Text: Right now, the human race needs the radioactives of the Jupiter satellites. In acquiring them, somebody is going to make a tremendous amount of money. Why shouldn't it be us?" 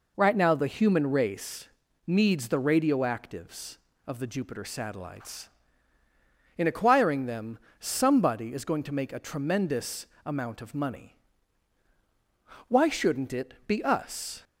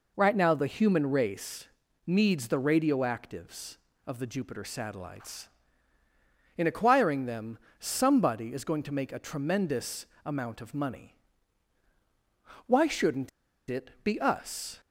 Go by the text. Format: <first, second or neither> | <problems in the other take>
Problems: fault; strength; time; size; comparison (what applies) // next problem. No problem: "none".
first | pauses between "race" and "needs"; at 1.6 s; 0.38 s long; also in the first // pauses between "tremendous" and "amount"; slight; at 10.0 s; 0.20 s long; slight in the first // pauses between "shouldn't" and "it"; at 13.2 s; 0.40 s long